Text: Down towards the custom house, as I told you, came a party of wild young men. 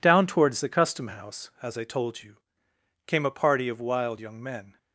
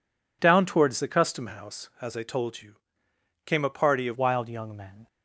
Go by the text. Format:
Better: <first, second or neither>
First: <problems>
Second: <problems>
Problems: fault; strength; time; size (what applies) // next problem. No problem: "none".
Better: first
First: none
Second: changes voice at "wild"; from 4.1 s on; 0.9 s long